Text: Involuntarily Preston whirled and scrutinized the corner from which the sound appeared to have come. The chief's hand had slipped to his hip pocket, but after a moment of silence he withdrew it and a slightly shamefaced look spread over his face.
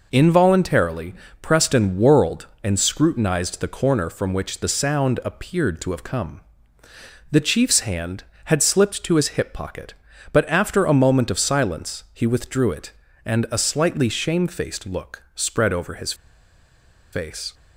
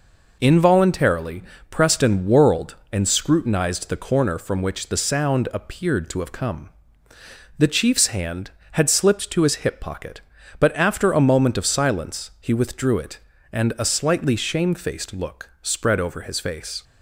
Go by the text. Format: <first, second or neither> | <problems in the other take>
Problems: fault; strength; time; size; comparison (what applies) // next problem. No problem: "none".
second | pauses between "Involuntarily" and "Preston"; slight; at 1.1 s; 0.28 s long; slight in the second // pauses between "his" and "face"; at 16.1 s; 0.99 s long